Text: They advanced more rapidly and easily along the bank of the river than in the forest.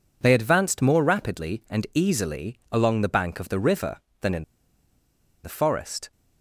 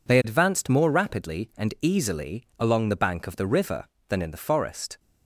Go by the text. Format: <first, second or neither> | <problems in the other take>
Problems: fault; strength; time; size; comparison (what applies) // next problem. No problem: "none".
second | pauses between "in" and "the"; at 4.4 s; 0.99 s long